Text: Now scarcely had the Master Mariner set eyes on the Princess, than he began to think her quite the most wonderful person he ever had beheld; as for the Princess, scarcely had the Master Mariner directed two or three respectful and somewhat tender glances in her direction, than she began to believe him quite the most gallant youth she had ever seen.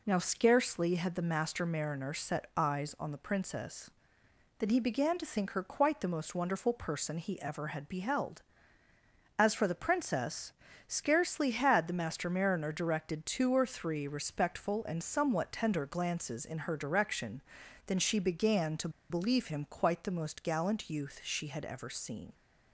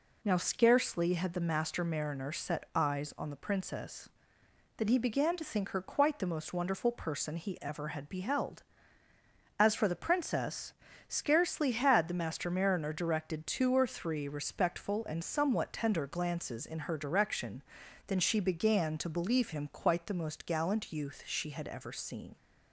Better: second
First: pauses between "to" and "believe"; slight; at 18.8 s; 0.20 s long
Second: none

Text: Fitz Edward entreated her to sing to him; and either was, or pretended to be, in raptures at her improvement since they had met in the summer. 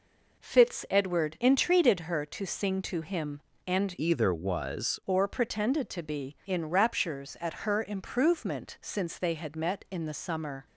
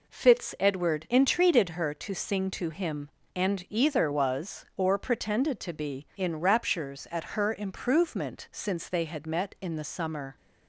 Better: second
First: changes voice from "either" to "was"; from 3.9 to 4.9 s; 1.0 s long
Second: none

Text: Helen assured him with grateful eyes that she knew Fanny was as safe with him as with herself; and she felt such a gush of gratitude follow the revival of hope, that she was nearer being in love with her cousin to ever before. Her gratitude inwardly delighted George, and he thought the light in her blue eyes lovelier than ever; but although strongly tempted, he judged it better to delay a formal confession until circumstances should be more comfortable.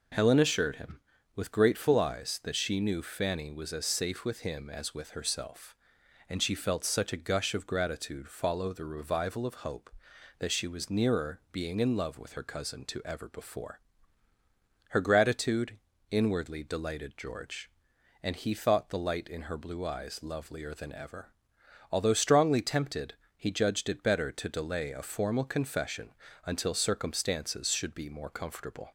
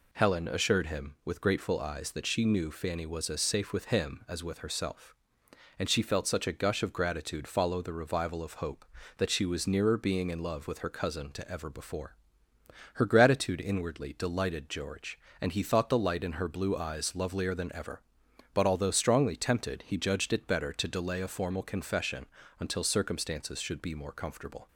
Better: second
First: pauses between "gratitude" and "inwardly"; slight; at 15.7 s; 0.32 s long // skips "but"; at 21.6 s // pauses between "confession" and "until"; slight; at 26.1 s; 0.34 s long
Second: pauses between "confession" and "until"; slight; at 22.2 s; 0.34 s long

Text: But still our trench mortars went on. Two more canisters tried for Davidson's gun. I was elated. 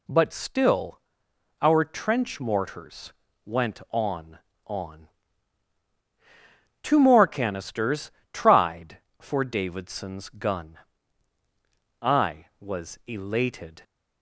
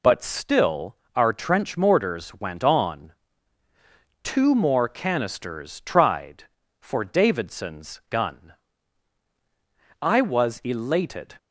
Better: second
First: pauses between "still" and "our"; noticeable; at 1.0 s; 0.59 s long // pauses between "mortars" and "went"; slight; at 3.1 s; 0.32 s long // says "on" twice; at 4.6 s // pauses between "canisters" and "tried"; slight; at 8.1 s; 0.22 s long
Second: pauses between "still" and "our"; slight; at 0.9 s; 0.18 s long

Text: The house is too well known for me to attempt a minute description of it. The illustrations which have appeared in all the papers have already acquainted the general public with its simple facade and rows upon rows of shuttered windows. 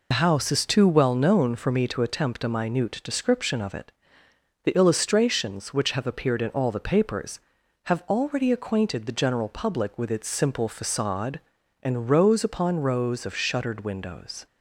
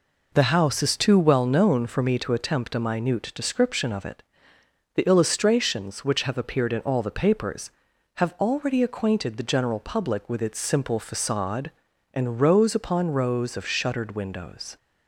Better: second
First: loses the start of "The"; at 0.1 s; 85 ms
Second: none

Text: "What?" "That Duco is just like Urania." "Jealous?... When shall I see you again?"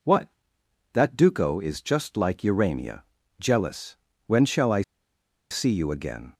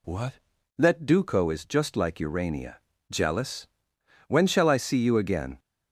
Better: second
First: pauses between "I" and "see"; noticeable; at 4.8 s; 0.69 s long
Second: none

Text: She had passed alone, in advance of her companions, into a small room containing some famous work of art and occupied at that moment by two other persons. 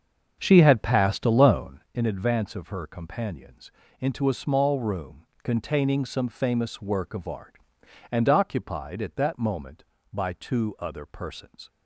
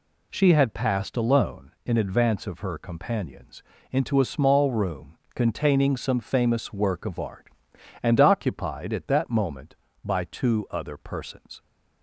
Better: second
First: starts louder than the rest; until 2.0 s; 6.5 dB // pauses between "room" and "containing"; slight; at 5.2 s; 0.18 s long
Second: pauses between "room" and "containing"; slight; at 5.1 s; 0.18 s long

